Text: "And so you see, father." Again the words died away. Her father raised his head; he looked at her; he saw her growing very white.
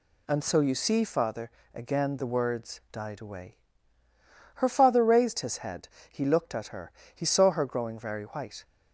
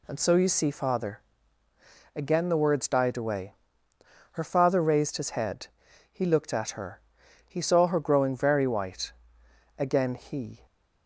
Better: first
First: none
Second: goes on to say "Again he"; noticeable; from 9.7 s on; 0.88 s long

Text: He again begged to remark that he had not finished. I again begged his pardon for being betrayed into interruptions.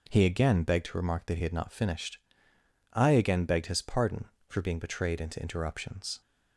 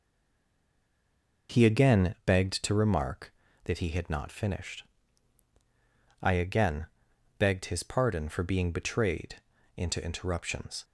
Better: first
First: none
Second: stays silent before the first word; noticeable; until 1.4 s; 1.4 s long // pauses between "again" and "begged"; noticeable; at 6.8 s; 0.54 s long // pauses between "betrayed" and "into"; slight; at 9.4 s; 0.34 s long

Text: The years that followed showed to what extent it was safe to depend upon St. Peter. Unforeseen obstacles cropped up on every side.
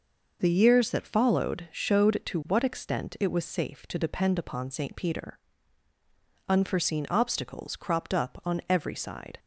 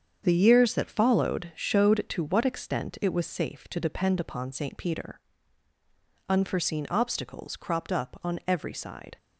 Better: first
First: none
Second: gets quieter; strong; throughout; 8 dB

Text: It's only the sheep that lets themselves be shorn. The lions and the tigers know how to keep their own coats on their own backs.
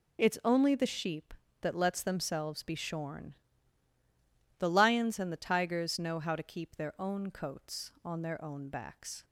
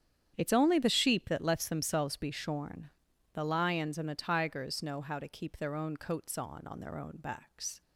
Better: first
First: none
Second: starts louder than the rest; strong; until 1.3 s; 9 dB // says "on" twice; at 6.6 s

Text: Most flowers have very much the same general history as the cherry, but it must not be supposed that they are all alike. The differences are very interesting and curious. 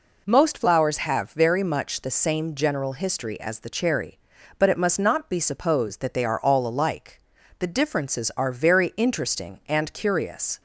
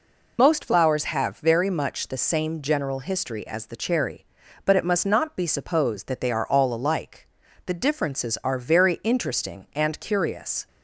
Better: first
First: none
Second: loses the start of "Most"; at 0.3 s; 60 ms

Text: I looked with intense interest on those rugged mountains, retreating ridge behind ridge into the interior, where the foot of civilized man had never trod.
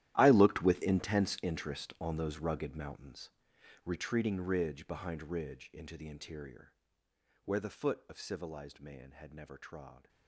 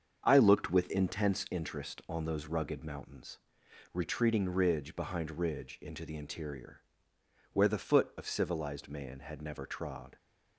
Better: second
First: gets quieter; strong; throughout; 17 dB // starts louder than the rest; strong; until 1.1 s; 13 dB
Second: starts louder than the rest; until 1.2 s; 7 dB

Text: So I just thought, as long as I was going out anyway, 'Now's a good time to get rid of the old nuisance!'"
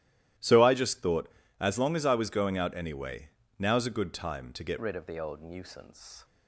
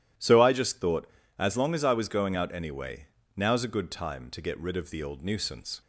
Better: second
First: starts louder than the rest; strong; until 1.7 s; 14 dB // changes voice at "rid"; from 4.8 s on; 1.4 s long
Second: none

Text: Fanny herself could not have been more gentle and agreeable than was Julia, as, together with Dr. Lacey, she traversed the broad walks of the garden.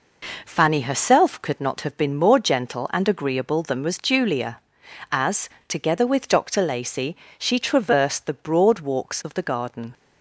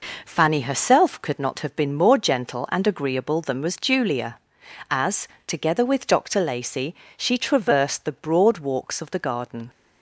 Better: neither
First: none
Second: none

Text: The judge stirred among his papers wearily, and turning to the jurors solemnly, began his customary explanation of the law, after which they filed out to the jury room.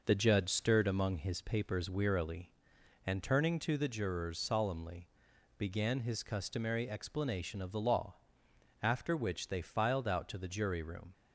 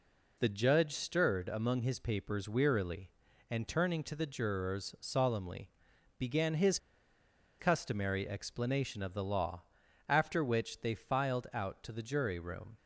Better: first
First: none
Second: pauses between "his" and "customary"; noticeable; at 6.7 s; 0.81 s long

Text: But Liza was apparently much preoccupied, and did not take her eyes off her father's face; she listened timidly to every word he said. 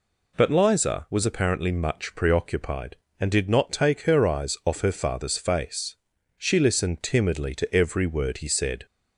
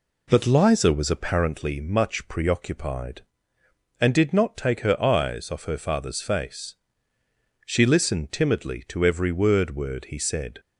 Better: first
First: none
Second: says "word" twice; at 9.7 s

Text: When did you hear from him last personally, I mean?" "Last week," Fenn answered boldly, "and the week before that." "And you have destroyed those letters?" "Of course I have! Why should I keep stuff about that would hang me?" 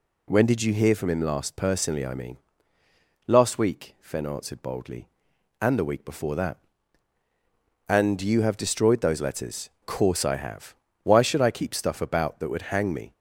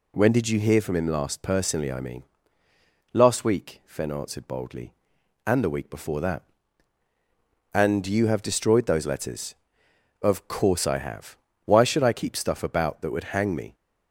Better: second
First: skips "Of"; at 9.7 s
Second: none

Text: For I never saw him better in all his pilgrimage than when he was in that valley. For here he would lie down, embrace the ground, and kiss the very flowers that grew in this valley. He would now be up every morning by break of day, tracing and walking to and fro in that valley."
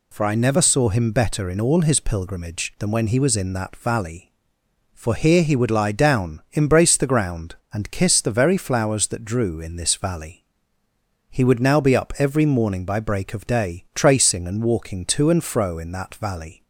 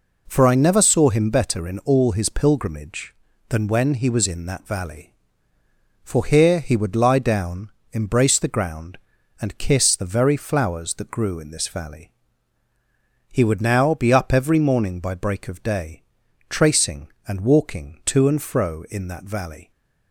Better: second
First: says "drew" for "grew"; at 9.2 s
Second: none

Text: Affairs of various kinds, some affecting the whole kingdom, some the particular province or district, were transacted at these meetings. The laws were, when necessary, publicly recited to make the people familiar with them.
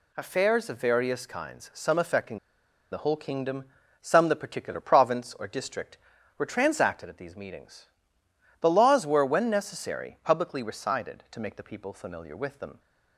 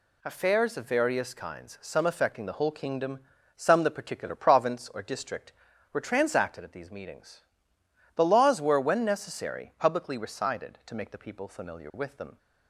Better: second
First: pauses between "affecting" and "the"; noticeable; at 2.3 s; 0.54 s long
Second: none

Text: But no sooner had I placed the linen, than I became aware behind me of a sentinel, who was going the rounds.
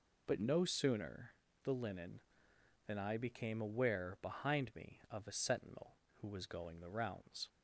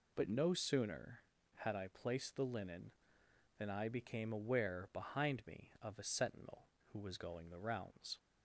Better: second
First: skips "had I placed"; at 1.4 s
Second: none

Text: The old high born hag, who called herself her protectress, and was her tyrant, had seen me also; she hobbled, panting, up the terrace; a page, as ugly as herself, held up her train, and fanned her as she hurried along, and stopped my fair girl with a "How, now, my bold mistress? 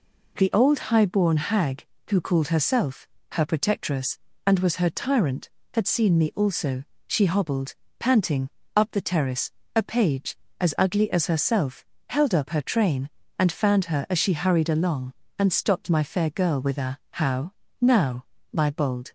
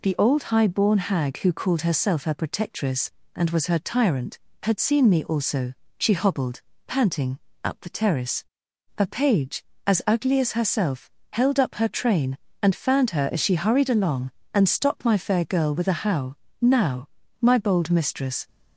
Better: second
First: pauses between "herself" and "her"; slight; at 3.0 s; 0.24 s long // stops before "mistress"; at 19.0 s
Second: none

